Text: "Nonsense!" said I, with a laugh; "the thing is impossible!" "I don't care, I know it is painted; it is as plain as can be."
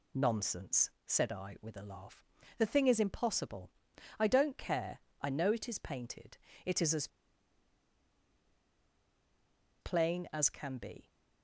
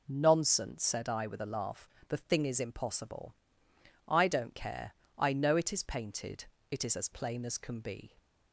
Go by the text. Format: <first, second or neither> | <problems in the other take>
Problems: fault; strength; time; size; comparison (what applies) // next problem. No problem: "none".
second | pauses between "as" and "plain"; strong; at 7.0 s; 2.7 s long